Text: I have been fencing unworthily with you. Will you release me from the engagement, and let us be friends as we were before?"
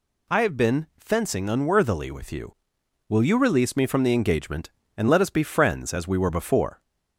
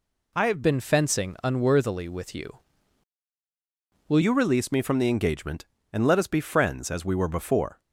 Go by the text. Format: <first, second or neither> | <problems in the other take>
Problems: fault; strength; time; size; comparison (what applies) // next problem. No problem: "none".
first | changes voice from "been" to "Will"; from 0.6 to 4.2 s; 3.6 s long